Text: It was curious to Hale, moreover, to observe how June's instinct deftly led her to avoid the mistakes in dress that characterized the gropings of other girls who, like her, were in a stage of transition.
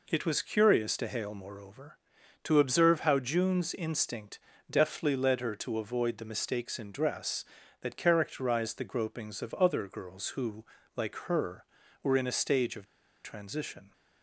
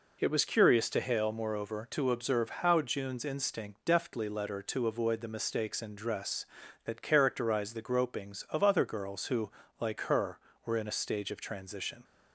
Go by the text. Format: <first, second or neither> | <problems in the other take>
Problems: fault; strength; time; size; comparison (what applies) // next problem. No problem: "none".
second | pauses between "instinct" and "deftly"; slight; at 4.3 s; 0.32 s long // pauses between "of" and "transition"; at 12.8 s; 0.38 s long